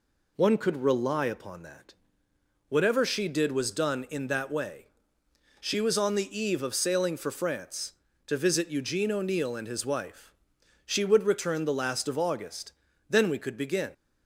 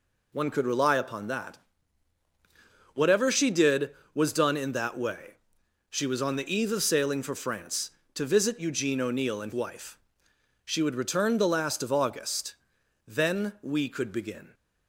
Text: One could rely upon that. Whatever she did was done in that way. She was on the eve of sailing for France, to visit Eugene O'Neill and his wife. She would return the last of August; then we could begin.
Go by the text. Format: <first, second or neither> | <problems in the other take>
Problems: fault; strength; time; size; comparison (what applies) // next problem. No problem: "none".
first | skips "his"; at 9.5 s